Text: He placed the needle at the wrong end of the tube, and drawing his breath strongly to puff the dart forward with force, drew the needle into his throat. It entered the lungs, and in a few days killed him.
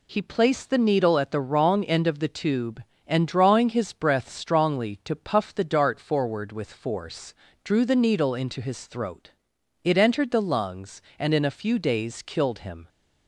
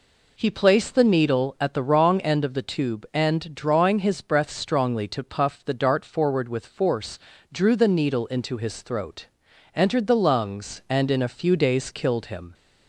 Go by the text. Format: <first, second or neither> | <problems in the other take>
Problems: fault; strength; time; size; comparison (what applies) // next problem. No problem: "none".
first | skips "It"; at 9.4 s